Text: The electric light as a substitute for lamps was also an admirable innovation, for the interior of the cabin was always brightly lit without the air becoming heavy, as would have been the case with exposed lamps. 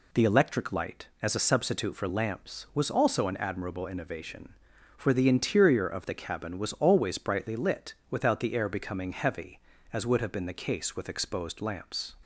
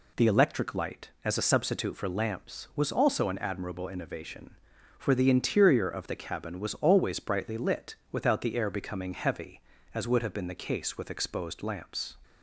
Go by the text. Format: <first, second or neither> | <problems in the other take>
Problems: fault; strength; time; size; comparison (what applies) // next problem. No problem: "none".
neither | pauses between "lit" and "without"; slight; the same in both